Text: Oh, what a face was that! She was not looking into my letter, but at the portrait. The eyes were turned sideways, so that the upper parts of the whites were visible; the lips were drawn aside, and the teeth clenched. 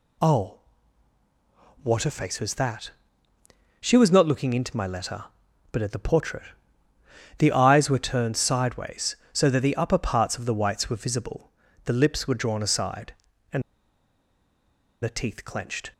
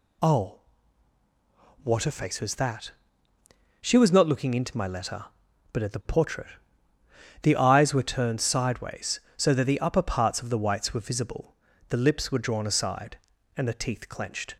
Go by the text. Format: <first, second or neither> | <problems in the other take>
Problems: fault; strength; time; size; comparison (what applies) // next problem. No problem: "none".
second | pauses between "and" and "the"; strong; at 13.6 s; 1.4 s long